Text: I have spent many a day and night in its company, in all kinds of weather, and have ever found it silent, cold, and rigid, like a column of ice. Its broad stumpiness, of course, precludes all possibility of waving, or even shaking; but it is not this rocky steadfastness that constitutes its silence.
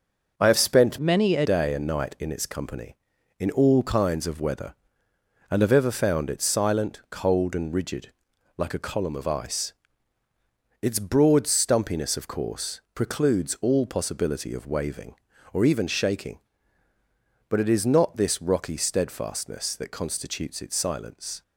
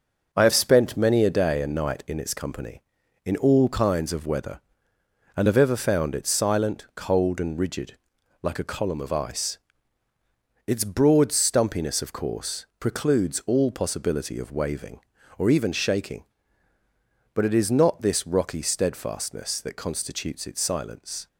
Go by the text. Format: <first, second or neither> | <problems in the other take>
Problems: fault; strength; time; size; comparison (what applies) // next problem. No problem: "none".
second | changes voice from "many" to "a"; from 0.9 to 1.4 s; 0.5 s long